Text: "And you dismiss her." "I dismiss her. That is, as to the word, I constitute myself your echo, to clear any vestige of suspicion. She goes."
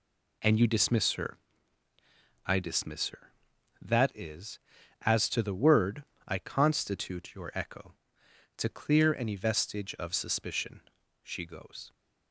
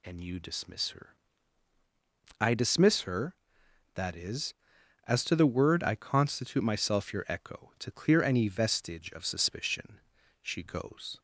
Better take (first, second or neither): second